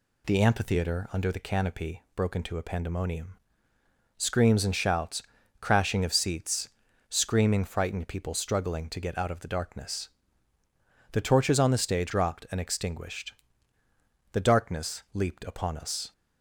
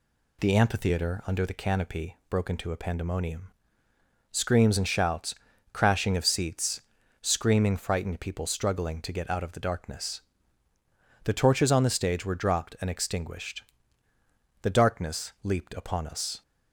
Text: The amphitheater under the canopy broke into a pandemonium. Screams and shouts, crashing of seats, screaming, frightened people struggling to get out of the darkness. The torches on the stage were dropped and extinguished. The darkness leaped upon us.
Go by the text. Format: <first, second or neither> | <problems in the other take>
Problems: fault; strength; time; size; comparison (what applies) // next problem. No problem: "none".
second | skips "were"; at 12.1 s